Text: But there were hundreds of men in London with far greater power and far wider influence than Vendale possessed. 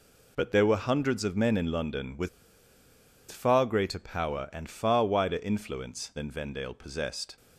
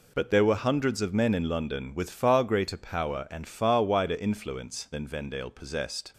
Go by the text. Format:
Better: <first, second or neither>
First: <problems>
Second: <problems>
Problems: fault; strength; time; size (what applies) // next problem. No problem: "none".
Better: second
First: pauses between "with" and "far"; at 2.2 s; 1.0 s long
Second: none